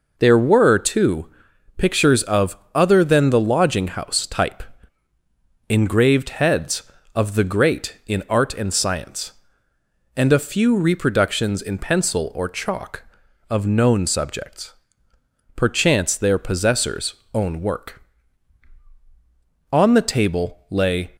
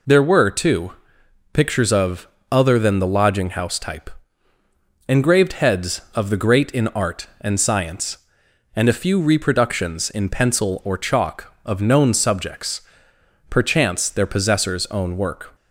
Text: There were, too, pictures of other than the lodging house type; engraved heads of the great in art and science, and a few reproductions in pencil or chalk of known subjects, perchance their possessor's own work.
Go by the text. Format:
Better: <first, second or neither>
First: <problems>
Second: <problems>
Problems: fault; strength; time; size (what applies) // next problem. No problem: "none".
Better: second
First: pauses between "of" and "other"; slight; at 2.5 s; 0.18 s long // pauses between "possessor's" and "own"; slight; at 17.1 s; 0.18 s long // goes on to say "On the table lay"; from 19.7 s on; 1.3 s long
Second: pauses between "of" and "other"; slight; at 2.2 s; 0.24 s long